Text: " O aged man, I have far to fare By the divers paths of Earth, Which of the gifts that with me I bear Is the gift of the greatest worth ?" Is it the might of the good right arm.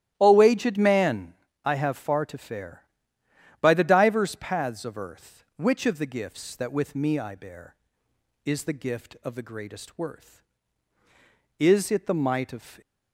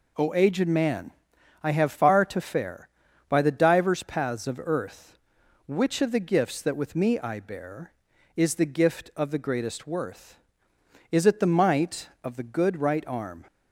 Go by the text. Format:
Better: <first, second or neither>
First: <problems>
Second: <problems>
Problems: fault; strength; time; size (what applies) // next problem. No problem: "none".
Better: second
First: starts louder than the rest; strong; until 1.1 s; 13 dB // stops before "the good right arm"; at 12.8 s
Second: none